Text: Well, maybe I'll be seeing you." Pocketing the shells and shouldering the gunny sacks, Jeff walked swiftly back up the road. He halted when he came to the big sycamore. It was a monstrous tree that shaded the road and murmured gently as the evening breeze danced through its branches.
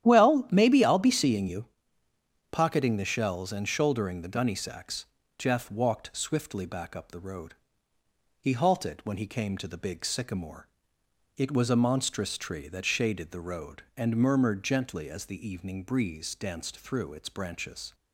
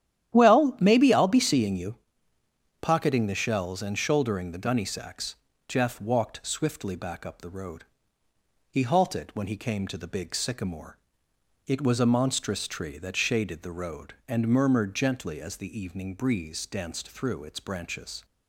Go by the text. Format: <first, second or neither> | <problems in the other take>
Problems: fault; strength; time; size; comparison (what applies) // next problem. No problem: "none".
neither | starts louder than the rest; strong; the same in both